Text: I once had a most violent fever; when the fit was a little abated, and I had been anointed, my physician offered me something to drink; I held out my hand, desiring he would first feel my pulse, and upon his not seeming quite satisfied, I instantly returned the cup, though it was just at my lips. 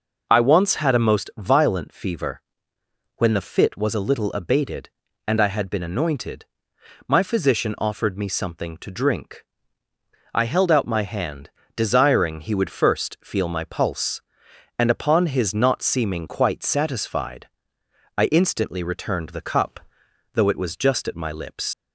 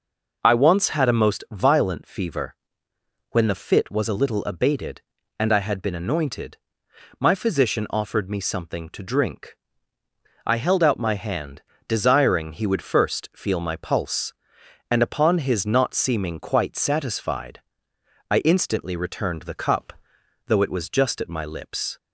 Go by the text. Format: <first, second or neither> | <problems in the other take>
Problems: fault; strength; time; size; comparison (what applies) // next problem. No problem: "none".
second | leaves "lips" unfinished; at 21.7 s; 100 ms